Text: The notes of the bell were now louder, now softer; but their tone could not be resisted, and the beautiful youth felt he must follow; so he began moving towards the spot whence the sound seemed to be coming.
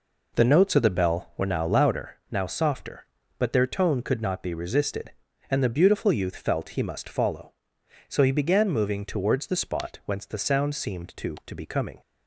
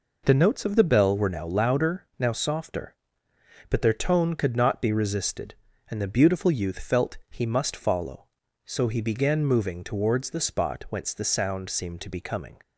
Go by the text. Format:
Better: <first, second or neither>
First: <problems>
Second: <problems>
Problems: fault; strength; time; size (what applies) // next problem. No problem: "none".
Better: second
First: says "to" twice; at 11.4 s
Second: none